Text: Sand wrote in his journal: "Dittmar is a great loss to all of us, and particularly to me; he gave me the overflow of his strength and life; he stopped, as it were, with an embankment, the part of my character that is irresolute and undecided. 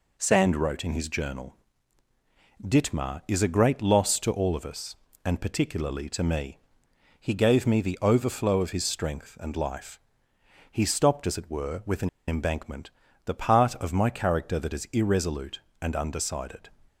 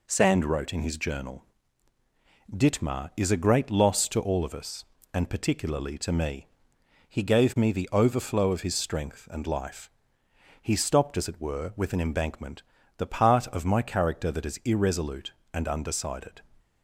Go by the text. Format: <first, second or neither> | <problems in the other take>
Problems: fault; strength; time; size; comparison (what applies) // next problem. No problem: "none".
second | pauses between "an" and "embankment"; slight; at 12.0 s; 0.18 s long